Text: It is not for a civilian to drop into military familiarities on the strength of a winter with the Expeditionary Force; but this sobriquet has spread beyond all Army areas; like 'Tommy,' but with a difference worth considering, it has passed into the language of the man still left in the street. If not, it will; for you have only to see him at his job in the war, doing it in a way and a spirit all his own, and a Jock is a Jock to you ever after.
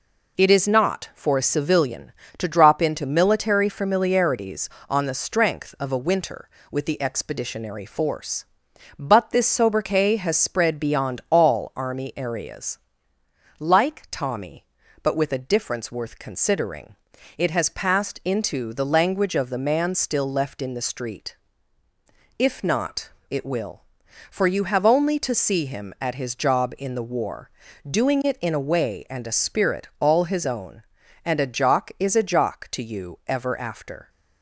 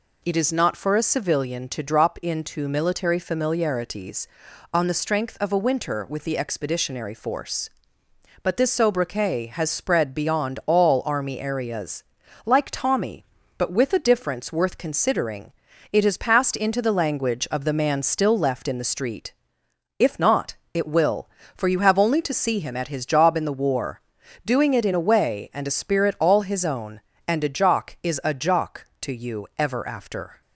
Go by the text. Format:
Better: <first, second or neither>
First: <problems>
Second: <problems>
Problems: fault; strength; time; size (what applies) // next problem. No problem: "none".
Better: neither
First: none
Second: none